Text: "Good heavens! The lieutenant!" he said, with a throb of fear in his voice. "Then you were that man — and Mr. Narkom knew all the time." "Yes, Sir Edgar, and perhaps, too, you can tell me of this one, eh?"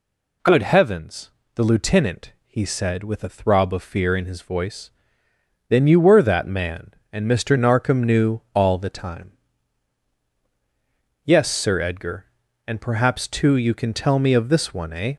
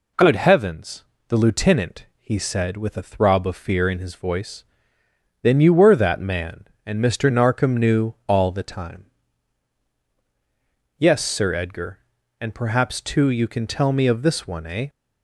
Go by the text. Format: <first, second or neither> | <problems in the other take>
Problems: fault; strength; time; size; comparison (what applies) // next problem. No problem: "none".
second | gets louder; slight; throughout; 3 dB